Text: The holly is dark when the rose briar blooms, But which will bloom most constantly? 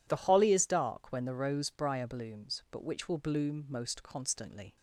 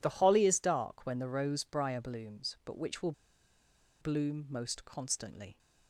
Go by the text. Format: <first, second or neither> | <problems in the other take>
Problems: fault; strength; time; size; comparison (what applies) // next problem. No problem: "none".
first | pauses between "will" and "bloom"; noticeable; at 3.1 s; 0.89 s long